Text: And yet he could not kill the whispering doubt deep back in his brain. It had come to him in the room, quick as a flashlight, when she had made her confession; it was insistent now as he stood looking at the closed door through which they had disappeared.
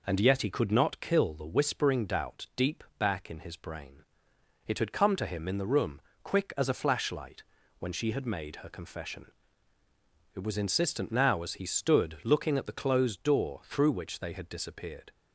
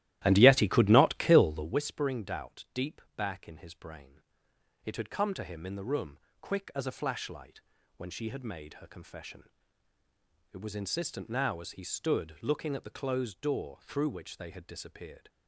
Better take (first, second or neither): first